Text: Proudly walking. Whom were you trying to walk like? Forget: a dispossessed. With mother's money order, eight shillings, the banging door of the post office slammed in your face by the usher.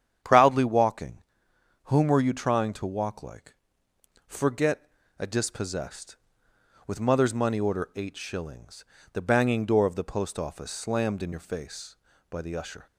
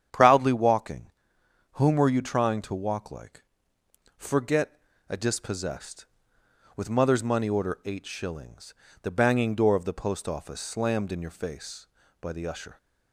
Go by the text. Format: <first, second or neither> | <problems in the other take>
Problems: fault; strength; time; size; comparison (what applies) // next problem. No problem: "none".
neither | starts louder than the rest; strong; the same in both